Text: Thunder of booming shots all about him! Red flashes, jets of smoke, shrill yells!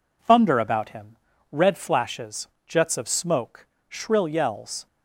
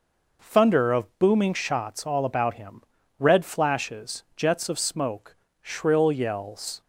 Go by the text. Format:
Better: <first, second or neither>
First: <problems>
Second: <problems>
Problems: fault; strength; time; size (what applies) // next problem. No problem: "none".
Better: second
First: skips "of booming shots all"; at 0.5 s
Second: none